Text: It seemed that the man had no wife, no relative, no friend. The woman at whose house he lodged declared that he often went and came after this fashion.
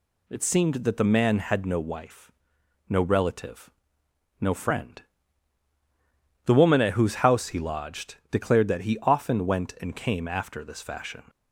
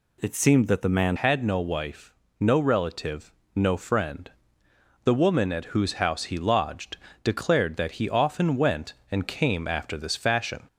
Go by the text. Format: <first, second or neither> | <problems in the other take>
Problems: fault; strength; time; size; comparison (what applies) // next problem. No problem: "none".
first | changes voice at "had"; from 1.1 s on; 9.5 s long // pauses between "lodged" and "declared"; slight; at 6.9 s; 0.26 s long